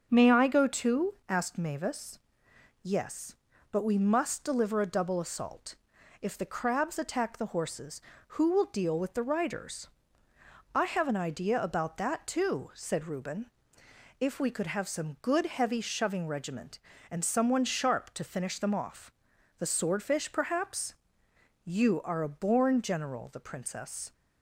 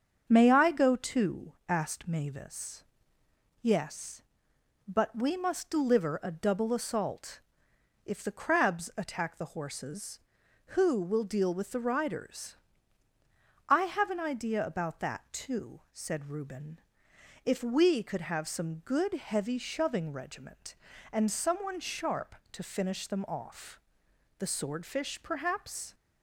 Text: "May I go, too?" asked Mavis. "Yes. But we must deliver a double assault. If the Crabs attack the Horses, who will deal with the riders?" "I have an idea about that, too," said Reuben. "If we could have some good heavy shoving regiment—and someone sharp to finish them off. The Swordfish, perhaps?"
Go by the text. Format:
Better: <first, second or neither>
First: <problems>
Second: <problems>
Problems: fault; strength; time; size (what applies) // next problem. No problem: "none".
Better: second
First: starts louder than the rest; until 1.1 s; 7 dB // goes on to say "You are a born general the Princess"; strong; from 21.6 s on; 2.4 s long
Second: starts louder than the rest; until 1.3 s; 7 dB